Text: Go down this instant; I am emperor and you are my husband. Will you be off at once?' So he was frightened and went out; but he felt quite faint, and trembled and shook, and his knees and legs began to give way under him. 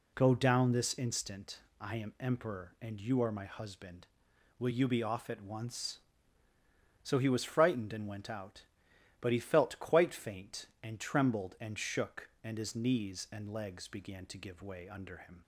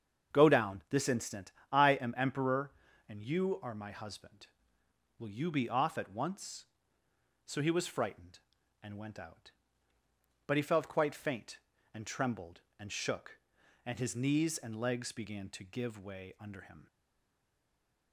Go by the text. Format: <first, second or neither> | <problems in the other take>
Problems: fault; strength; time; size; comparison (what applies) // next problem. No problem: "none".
first | starts louder than the rest; strong; until 1.3 s; 7 dB // stays silent after the last word; noticeable; from 16.8 s on; 1.3 s long